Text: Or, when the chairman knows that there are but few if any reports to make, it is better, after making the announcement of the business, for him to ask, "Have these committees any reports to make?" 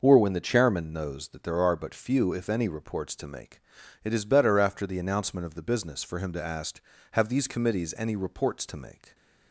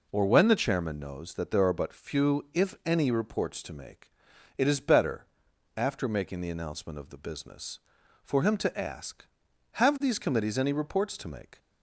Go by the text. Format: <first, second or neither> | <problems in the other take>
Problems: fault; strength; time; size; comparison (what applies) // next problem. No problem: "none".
second | skips "making"; at 4.8 s